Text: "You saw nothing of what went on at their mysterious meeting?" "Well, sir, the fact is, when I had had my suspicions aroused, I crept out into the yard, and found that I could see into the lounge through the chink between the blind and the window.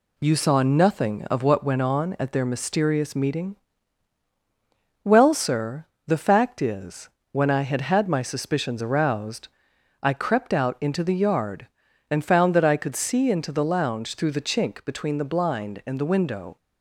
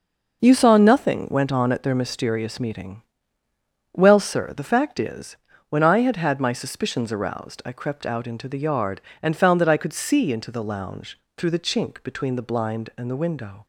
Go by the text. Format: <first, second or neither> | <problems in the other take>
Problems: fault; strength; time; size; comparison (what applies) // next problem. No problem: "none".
first | skips "of what"; at 1.2 s // pauses between "lounge" and "through"; slight; at 11.1 s; 0.16 s long